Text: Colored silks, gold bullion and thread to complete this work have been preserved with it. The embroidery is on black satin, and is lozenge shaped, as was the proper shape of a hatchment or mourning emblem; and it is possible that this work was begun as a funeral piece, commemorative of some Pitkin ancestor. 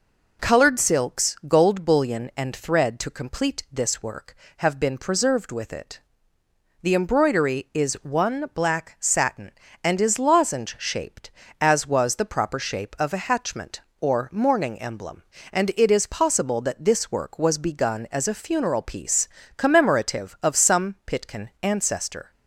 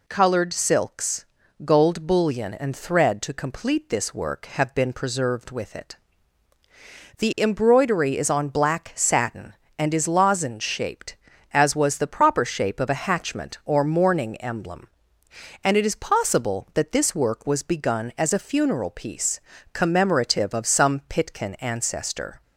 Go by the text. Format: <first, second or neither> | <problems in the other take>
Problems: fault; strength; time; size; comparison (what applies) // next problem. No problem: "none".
second | says "one" for "on"; at 8.0 s